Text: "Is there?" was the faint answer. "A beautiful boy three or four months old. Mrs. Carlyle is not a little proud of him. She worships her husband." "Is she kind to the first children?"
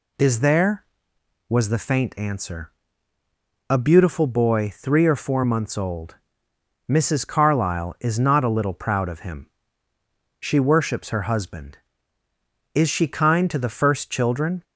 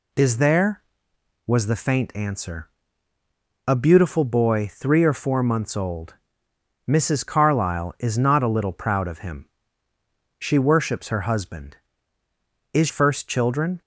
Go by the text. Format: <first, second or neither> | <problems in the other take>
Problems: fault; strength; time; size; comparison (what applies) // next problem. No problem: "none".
first | skips "she kind to the"; at 12.8 s